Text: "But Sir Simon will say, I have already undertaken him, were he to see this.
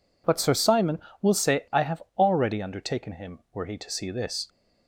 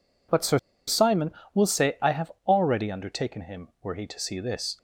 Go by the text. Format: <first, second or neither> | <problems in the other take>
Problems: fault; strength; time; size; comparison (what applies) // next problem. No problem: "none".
first | pauses between "Sir" and "Simon"; slight; at 0.5 s; 0.27 s long // pauses between "have" and "already"; slight; at 2.3 s; 0.16 s long; slight in the first